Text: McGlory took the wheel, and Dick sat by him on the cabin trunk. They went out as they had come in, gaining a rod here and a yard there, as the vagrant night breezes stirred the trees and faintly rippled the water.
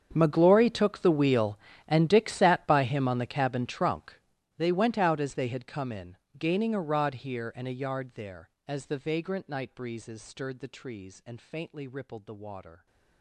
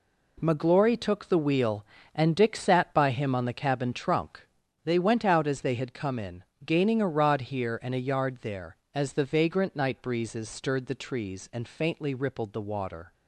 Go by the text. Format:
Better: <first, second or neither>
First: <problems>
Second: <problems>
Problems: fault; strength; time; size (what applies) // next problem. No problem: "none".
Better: second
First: gets quieter; strong; throughout; 21 dB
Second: none